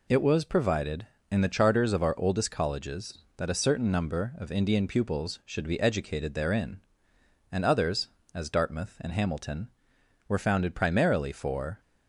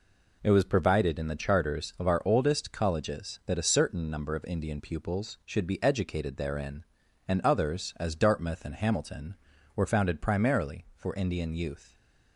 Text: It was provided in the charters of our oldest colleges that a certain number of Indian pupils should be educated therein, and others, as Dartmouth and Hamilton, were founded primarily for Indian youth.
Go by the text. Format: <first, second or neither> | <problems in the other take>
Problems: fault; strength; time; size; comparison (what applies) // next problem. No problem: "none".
second | stops before "Indian youth"; at 11.7 s